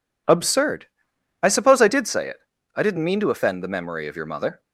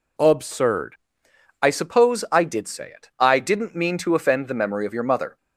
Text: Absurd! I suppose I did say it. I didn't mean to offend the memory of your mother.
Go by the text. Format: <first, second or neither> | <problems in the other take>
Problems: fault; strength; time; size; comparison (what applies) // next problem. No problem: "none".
neither | none